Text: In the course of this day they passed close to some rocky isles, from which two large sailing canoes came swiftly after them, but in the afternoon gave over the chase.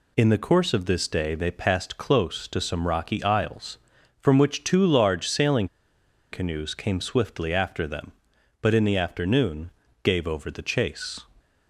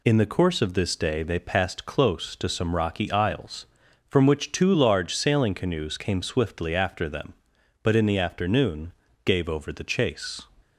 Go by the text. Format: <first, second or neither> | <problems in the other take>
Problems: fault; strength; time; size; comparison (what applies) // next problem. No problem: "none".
second | pauses between "sailing" and "canoes"; noticeable; at 5.6 s; 0.63 s long // pauses between "afternoon" and "gave"; slight; at 9.6 s; 0.32 s long; slight in the second